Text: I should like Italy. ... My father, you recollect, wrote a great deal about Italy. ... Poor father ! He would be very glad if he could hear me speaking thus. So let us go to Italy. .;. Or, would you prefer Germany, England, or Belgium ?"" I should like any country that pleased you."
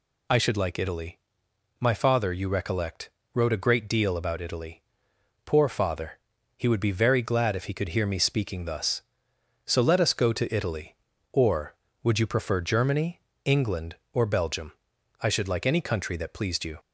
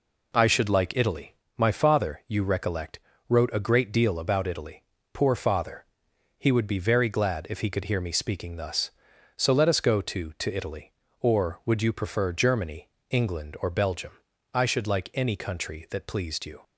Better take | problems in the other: first | says "to" twice; at 10.3 s

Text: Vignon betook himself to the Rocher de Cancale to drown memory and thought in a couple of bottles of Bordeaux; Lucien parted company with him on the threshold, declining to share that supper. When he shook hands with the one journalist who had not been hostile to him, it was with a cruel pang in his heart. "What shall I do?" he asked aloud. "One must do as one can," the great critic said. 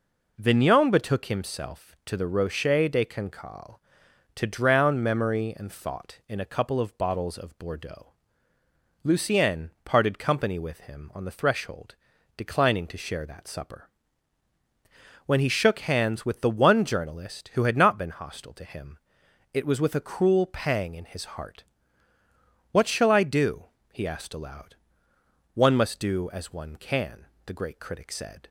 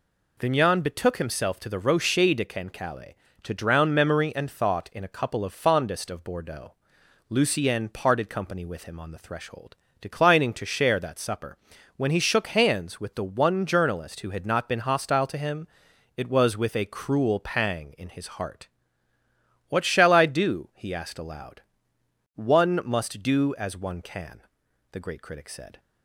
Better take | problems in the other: first | says "fondest" for "bottles"; at 5.5 s

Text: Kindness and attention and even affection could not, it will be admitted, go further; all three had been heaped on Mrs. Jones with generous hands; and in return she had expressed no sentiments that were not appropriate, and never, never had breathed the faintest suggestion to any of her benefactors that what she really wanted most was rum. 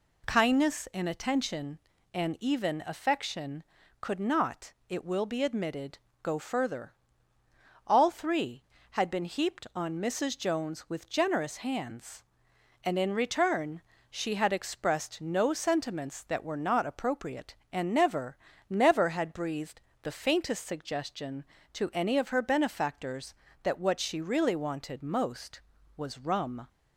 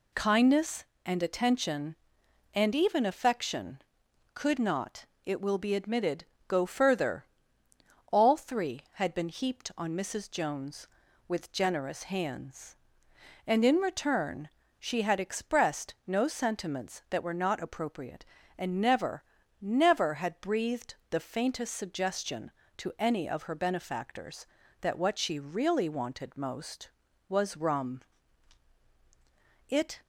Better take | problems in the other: first | pauses between "return" and "she"; slight; at 14.4 s; 0.29 s long; slight in the first // pauses between "breathed" and "the"; slight; at 20.9 s; 0.16 s long; slight in the first // goes on to say "It"; slight; from 29.6 s on; 0.32 s long

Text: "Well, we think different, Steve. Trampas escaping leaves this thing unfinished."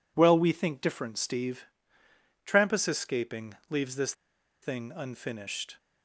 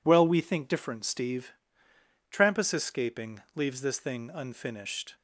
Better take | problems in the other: second | pauses between "escaping" and "leaves"; slight; at 3.5 s; 0.16 s long; slight in the second // pauses between "this" and "thing"; noticeable; at 4.1 s; 0.50 s long

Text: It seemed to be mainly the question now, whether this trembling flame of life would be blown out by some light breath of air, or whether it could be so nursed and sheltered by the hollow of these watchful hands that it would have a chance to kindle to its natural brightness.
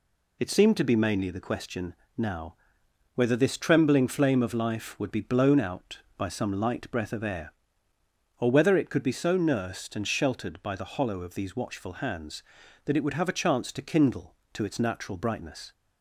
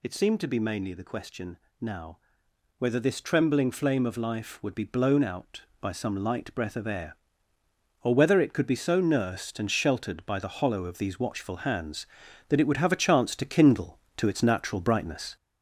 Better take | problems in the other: first | gets louder; noticeable; throughout; 4.5 dB // pauses between "question" and "now"; slight; at 1.5 s; 0.22 s long; slight in the first

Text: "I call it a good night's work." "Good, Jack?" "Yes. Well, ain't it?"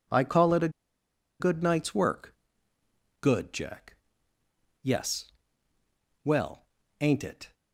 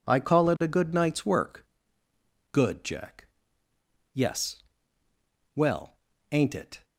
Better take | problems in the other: second | pauses between "a" and "good"; noticeable; at 0.6 s; 0.70 s long

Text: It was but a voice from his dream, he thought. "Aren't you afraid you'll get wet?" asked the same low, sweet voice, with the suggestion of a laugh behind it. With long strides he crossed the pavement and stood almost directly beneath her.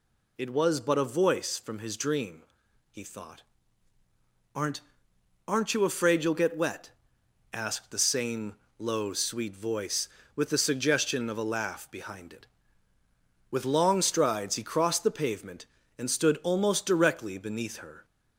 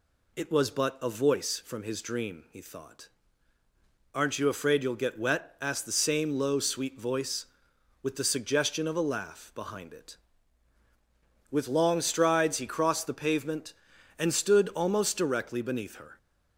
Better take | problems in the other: second | says "Aren't" twice; at 5.4 s // pauses between "same" and "low"; slight; at 8.5 s; 0.22 s long

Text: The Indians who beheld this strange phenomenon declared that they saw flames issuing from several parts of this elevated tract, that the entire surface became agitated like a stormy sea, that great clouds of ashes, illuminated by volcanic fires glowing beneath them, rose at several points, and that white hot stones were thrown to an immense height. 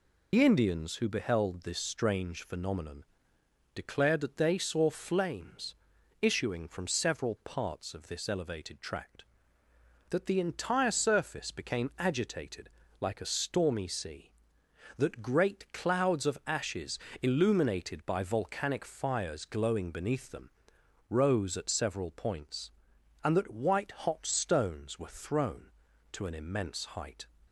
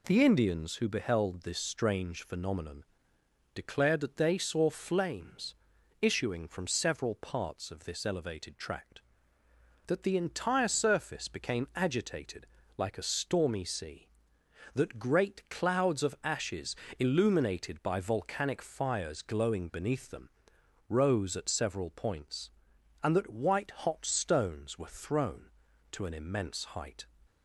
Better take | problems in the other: second | loses the start of "The"; at 0.3 s; 85 ms // pauses between "phenomenon" and "declared"; noticeable; at 3.0 s; 0.72 s long; noticeable in the second // pauses between "flames" and "issuing"; at 5.7 s; 0.44 s long; also in the second // pauses between "agitated" and "like"; slight; at 12.6 s; 0.32 s long; slight in the second

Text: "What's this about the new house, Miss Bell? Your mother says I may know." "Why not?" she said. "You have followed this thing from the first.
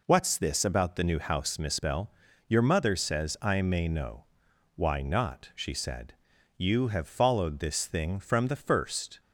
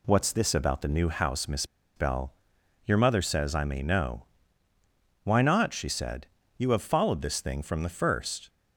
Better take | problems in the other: first | pauses between "Miss" and "Bell"; slight; at 1.6 s; 0.30 s long

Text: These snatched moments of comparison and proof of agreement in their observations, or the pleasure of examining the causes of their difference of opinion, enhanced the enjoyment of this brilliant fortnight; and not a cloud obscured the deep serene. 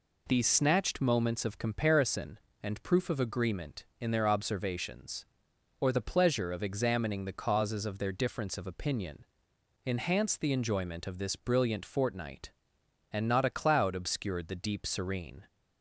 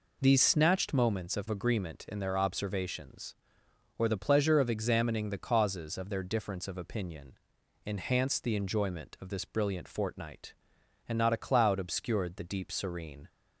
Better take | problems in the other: first | skips "comparison and proof of"; at 1.4 s

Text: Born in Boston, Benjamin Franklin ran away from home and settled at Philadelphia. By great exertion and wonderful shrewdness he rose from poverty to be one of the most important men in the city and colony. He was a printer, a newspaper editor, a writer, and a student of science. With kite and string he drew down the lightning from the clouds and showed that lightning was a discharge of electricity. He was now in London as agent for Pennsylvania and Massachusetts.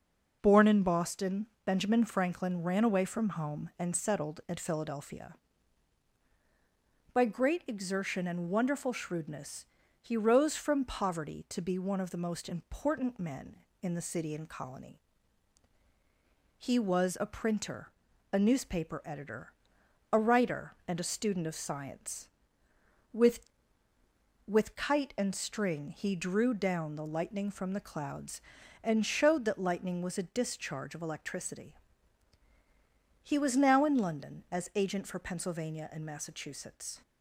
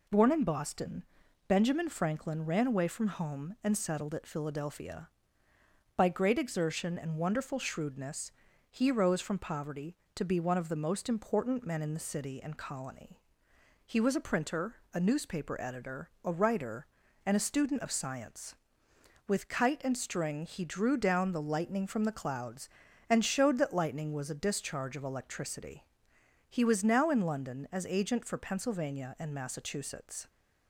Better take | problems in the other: second | pauses between "shrewdness" and "he"; slight; at 9.6 s; 0.36 s long; also in the second // says "With" twice; at 24.4 s

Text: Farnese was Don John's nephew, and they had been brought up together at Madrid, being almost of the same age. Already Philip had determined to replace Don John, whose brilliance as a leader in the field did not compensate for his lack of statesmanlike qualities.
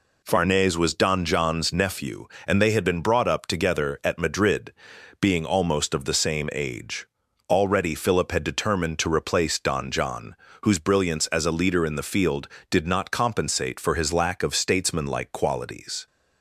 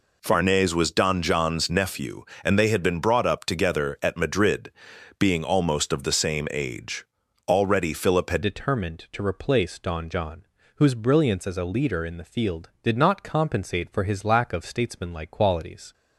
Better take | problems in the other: first | changes voice at "determined"; from 8.4 s on; 7.5 s long

